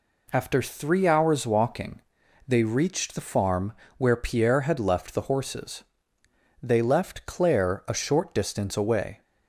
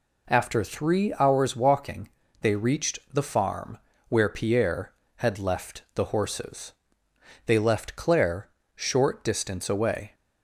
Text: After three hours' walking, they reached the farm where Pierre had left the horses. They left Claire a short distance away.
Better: first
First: pauses between "farm" and "where"; slight; at 3.7 s; 0.24 s long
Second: pauses between "farm" and "where"; slight; at 3.7 s; 0.30 s long // skips "a"; at 8.6 s

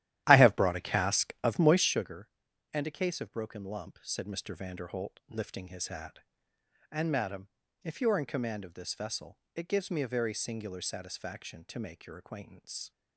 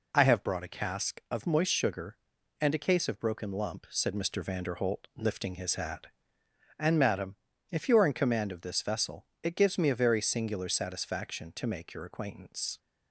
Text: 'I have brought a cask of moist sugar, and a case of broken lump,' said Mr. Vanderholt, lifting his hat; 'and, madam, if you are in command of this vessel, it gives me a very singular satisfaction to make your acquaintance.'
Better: second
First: starts louder than the rest; strong; until 2.1 s; 13 dB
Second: none

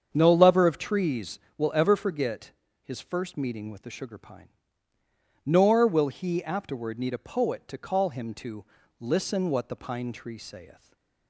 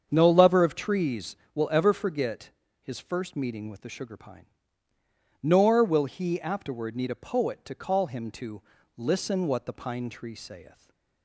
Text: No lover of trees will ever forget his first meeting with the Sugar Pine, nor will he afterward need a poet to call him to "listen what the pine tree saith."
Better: neither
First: starts louder than the rest; strong; until 1.1 s; 7.5 dB // pauses between "forget" and "his"; slight; at 2.5 s; 0.30 s long // pauses between "to" and "listen"; at 8.6 s; 0.38 s long // stays silent after the last word; slight; from 10.7 s on; 0.5 s long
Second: starts louder than the rest; strong; until 1.1 s; 7.5 dB // pauses between "forget" and "his"; slight; at 2.4 s; 0.30 s long // pauses between "to" and "listen"; at 8.6 s; 0.38 s long // stays silent after the last word; slight; from 10.6 s on; 0.6 s long

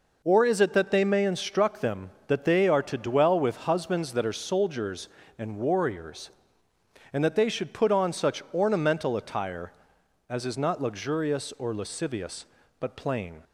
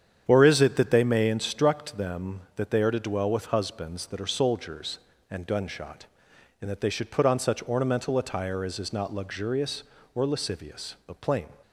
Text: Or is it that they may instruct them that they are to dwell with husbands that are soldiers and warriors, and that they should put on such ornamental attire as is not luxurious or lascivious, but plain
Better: first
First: none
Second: starts louder than the rest; strong; until 1.2 s; 8.5 dB // says "gunshot" for "warriors"; at 5.4 s

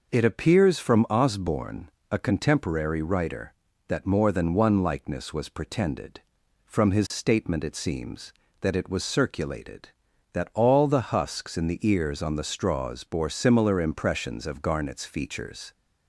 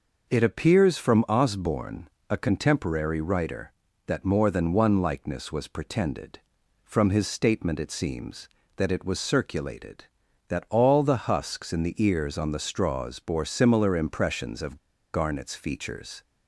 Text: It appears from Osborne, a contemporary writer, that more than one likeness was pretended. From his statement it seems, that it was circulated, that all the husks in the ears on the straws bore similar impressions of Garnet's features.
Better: first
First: none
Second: pauses between "of" and "Garnet's"; at 14.7 s; 0.37 s long

